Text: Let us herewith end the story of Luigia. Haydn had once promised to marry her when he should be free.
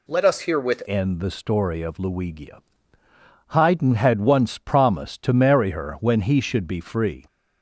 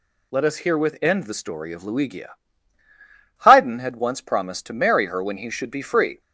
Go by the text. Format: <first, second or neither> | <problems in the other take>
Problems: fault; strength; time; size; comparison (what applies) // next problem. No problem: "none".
second | changes voice at "end"; from 0.8 s on; 6.4 s long